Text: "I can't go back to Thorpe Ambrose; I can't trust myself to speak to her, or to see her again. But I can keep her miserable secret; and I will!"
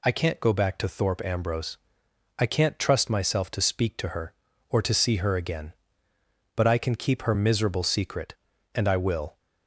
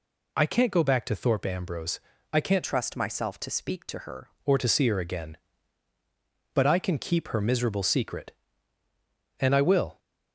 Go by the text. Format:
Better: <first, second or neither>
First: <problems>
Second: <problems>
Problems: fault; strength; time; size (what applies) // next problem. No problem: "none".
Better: first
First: none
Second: changes voice from "trust" to "her"; from 2.6 to 4.3 s; 1.7 s long